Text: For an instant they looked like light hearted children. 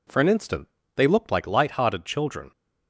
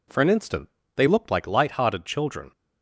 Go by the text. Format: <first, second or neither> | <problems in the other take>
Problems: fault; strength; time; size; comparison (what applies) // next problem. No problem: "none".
neither | pauses between "instant" and "they"; slight; the same in both